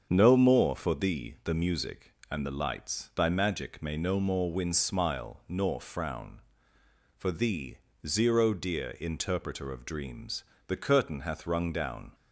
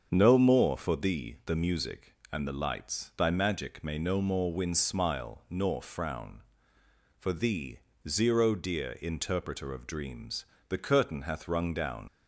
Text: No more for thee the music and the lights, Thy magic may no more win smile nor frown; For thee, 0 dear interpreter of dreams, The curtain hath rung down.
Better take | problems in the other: first | starts louder than the rest; until 1.1 s; 6.5 dB; also in the first // leaves "down" unfinished; at 12.0 s; 75 ms

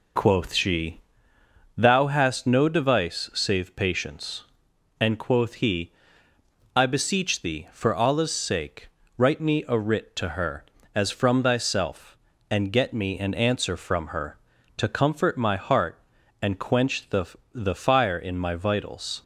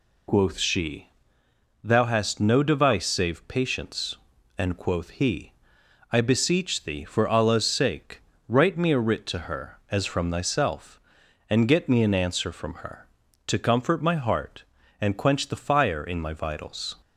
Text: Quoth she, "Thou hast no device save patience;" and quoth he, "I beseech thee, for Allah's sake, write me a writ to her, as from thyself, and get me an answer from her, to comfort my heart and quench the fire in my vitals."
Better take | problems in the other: second | says "the" twice; at 17.5 s

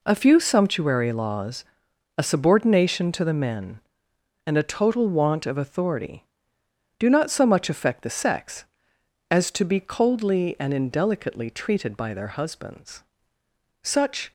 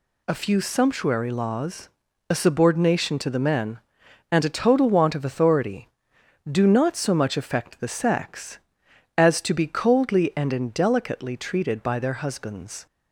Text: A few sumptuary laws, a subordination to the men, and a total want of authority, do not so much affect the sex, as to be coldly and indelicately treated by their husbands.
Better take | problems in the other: second | goes on to say "Such"; slight; from 13.8 s on; 0.48 s long

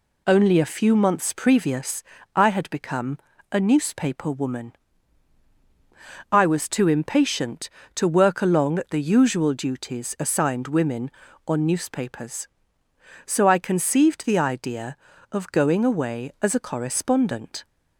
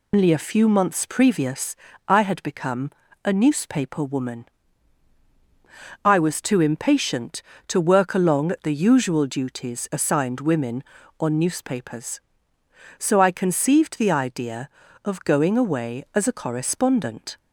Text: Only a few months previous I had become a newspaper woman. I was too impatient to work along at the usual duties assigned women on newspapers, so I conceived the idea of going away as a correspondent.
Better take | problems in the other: first | loses the start of "Only"; at 0.1 s; 145 ms // pauses between "previous" and "I"; slight; at 1.7 s; 0.32 s long; slight in the first // pauses between "become" and "a"; slight; at 2.8 s; 0.34 s long; slight in the first

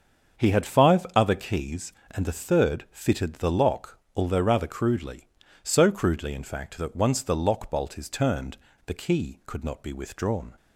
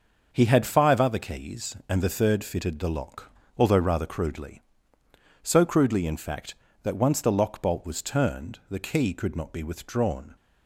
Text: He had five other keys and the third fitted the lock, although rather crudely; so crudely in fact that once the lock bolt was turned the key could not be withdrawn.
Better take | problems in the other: second | starts louder than the rest; until 1.4 s; 7 dB; also in the second // says "is" for "was"; at 7.9 s // pauses between "turned" and "the"; slight; at 8.5 s; 0.29 s long

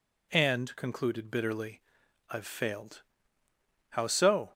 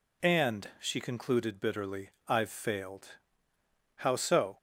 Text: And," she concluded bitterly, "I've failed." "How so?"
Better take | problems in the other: second | skips "she"; at 0.7 s

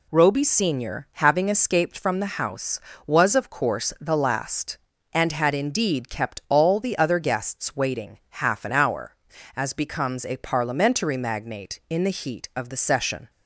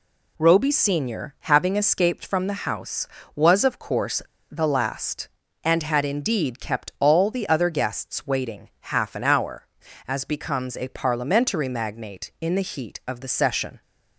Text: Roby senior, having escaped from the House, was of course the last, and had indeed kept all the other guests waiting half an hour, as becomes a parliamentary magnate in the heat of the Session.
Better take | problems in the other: first | pauses between "course" and "the"; slight; at 4.2 s; 0.29 s long

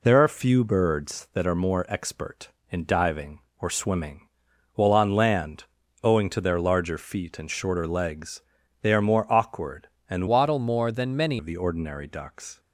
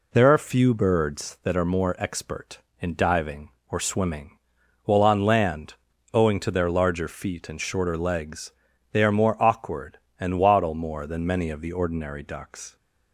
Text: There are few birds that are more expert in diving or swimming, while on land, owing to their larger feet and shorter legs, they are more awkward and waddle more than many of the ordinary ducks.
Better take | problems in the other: second | changes voice from "waddle" to "many"; from 10.2 to 11.3 s; 1.1 s long

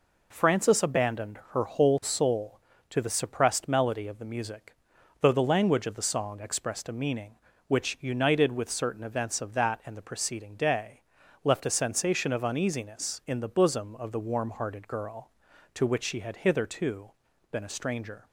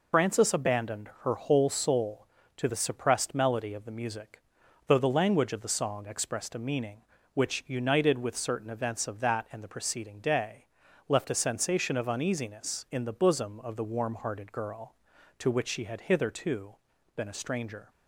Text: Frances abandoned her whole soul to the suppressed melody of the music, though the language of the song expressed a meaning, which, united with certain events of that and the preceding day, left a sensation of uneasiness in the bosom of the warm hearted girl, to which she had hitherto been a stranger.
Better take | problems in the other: first | loses the start of "Frances"; at 0.1 s; 125 ms // pauses between "hitherto" and "been"; at 16.7 s; 0.42 s long; also in the first

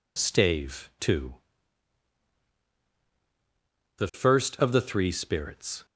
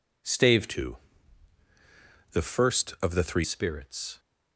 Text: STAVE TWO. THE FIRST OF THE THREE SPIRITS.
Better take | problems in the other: first | changes voice from "TWO" to "THREE"; from 0.6 to 3.4 s; 2.8 s long

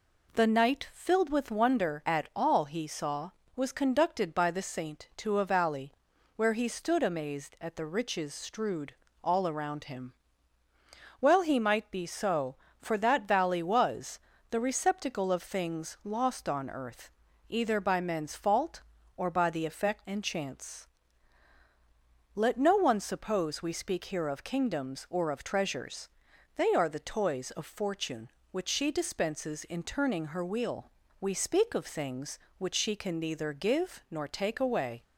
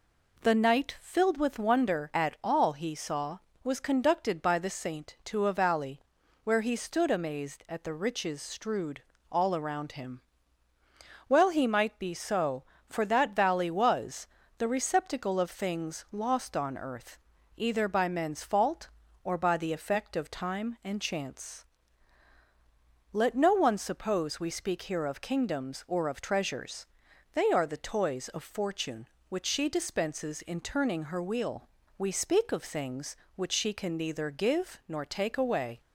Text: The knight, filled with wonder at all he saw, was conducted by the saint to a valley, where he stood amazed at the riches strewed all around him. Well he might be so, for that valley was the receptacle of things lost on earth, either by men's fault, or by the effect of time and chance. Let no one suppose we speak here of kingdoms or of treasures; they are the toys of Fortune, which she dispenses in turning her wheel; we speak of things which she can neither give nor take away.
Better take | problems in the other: second | pauses between "strewed" and "all"; slight; at 8.9 s; 0.30 s long; slight in the second // pauses between "was" and "the"; slight; at 14.1 s; 0.30 s long; slight in the second // skips "of time"; at 20.0 s

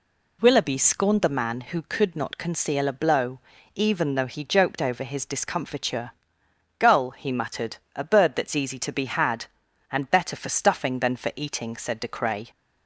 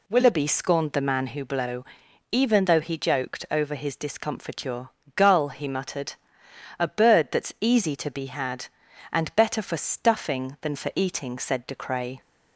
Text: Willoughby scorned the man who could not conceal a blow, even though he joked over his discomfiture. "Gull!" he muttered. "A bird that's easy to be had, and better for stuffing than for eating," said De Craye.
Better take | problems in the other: first | skips "could not conceal a"; at 1.4 s

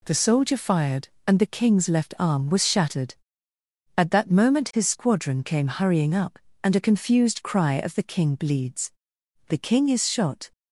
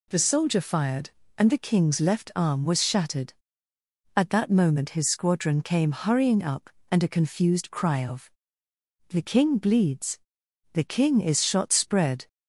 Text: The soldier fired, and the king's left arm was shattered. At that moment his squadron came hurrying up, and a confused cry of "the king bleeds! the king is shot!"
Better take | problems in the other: first | pauses between "of" and "the"; noticeable; at 8.2 s; 0.80 s long // goes on to say "spread"; from 11.7 s on; 0.56 s long

